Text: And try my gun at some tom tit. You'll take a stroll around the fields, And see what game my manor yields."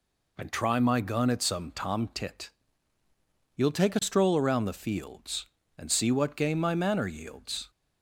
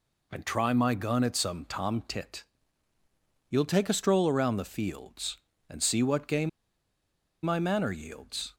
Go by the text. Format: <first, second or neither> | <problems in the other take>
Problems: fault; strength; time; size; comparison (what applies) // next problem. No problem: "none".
first | pauses between "game" and "my"; noticeable; at 6.4 s; 0.94 s long